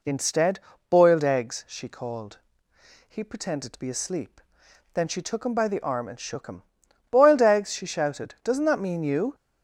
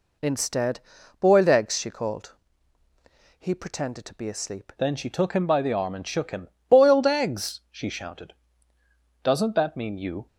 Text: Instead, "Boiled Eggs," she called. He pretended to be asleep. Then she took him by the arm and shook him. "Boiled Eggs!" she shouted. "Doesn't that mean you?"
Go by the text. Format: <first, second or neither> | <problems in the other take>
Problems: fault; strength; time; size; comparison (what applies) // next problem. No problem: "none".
first | changes voice at "Then"; from 4.7 s on; 5.5 s long